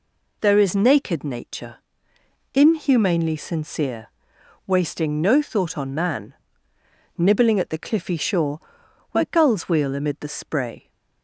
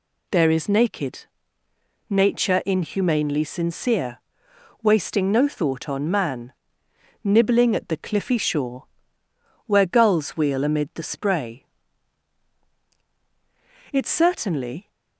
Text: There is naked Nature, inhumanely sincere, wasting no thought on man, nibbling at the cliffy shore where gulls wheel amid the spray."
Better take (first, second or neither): first